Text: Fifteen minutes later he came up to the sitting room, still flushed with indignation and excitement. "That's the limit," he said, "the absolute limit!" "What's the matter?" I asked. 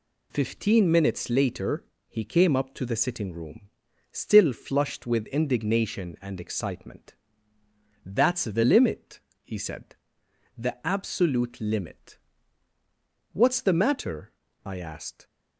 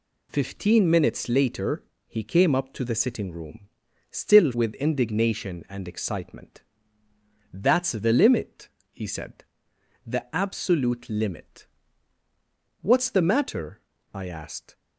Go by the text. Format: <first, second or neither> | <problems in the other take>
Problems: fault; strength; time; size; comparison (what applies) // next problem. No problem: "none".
first | pauses between "later" and "he"; slight; at 1.8 s; 0.24 s long; slight in the first // skips "flushed"; at 4.5 s